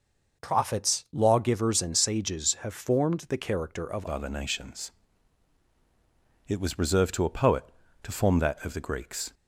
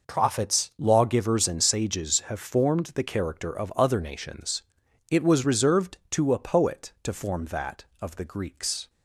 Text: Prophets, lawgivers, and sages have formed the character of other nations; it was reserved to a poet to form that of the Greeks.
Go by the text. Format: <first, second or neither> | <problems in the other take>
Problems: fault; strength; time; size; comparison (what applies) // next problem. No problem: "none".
second | changes voice at "other"; from 4.0 s on; 5.3 s long